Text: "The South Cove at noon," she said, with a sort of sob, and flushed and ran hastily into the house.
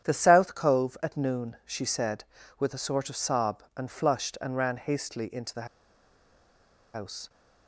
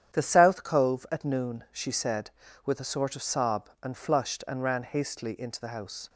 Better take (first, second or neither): second